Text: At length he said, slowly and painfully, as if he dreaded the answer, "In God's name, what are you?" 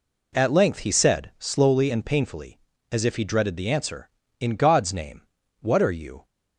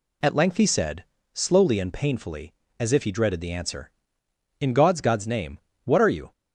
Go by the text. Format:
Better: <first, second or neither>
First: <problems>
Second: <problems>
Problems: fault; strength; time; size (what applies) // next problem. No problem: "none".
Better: first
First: none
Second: says "God's" twice; at 4.9 s